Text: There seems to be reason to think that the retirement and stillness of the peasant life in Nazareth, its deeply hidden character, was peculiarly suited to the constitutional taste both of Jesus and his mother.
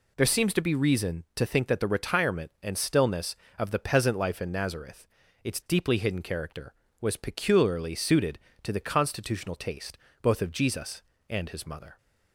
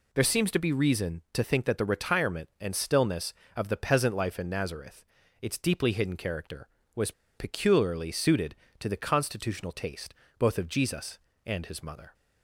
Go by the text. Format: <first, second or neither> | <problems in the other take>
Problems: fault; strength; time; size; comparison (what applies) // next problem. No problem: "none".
first | pauses between "was" and "peculiarly"; slight; at 7.1 s; 0.24 s long // pauses between "taste" and "both"; slight; at 10.1 s; 0.24 s long; slight in the first